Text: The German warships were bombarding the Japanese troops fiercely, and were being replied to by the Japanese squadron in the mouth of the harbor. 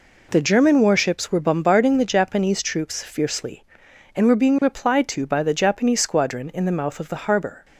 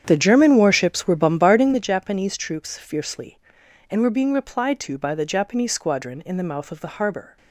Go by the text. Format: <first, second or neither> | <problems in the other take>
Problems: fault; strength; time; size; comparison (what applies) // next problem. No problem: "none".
first | starts louder than the rest; strong; until 1.9 s; 8.5 dB